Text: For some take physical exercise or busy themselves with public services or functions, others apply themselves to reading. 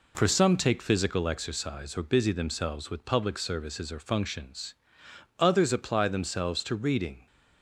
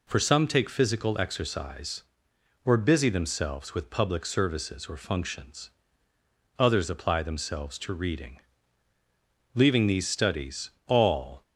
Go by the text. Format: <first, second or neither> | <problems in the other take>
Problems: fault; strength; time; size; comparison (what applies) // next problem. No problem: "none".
first | goes on to say "Leaving these studies all"; strong; from 9.5 s on; 1.8 s long